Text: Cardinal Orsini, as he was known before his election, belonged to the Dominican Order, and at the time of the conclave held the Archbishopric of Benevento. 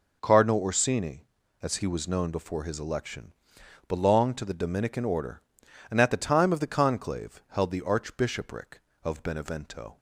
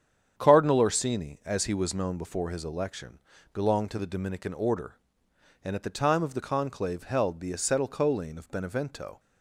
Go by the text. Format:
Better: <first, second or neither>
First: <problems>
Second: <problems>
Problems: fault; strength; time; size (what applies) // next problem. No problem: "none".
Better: first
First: none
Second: starts louder than the rest; strong; until 1.3 s; 8.5 dB // says "Acetylcholine" for "Archbishopric"; at 7.5 s